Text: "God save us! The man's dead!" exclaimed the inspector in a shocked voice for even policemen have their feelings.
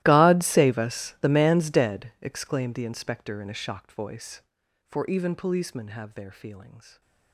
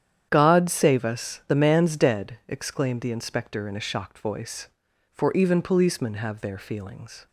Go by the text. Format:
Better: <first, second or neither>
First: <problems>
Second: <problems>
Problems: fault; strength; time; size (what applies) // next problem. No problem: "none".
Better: second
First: gets quieter; strong; throughout; 23 dB // starts louder than the rest; strong; until 1.0 s; 16 dB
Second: starts louder than the rest; strong; until 1.3 s; 9.5 dB